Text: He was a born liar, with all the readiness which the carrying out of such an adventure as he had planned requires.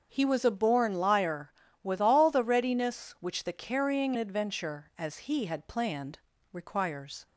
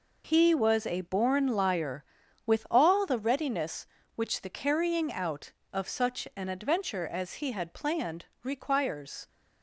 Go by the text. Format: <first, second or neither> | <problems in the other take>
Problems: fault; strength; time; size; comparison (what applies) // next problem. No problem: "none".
second | starts louder than the rest; until 1.1 s; 7 dB // skips "out of such an"; at 4.1 s // pauses between "planned" and "requires"; slight; at 6.1 s; 0.32 s long; slight in the second